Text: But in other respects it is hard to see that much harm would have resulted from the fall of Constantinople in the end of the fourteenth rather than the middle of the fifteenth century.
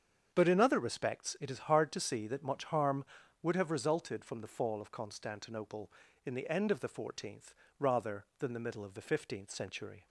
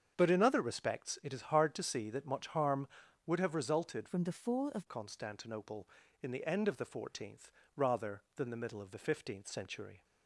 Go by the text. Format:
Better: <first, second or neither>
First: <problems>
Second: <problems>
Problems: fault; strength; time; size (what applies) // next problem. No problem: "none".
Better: first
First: starts louder than the rest; strong; until 1.3 s; 7.5 dB // pauses between "fourteenth" and "rather"; slight; at 7.5 s; 0.24 s long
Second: starts louder than the rest; strong; until 1.1 s; 7.5 dB // changes voice from "from" to "of"; from 4.0 to 4.8 s; 0.8 s long // pauses between "fourteenth" and "rather"; slight; at 7.5 s; 0.24 s long